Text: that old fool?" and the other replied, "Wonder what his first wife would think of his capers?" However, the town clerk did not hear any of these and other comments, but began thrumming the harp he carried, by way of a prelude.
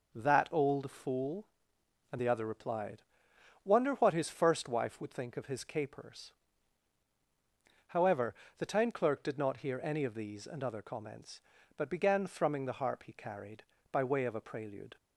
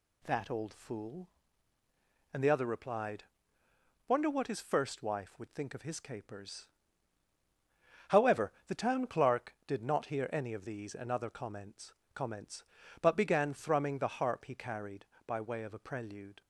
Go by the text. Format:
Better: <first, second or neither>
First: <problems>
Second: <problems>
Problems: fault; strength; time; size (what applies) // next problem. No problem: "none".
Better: first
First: none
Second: says "comments" twice; at 12.1 s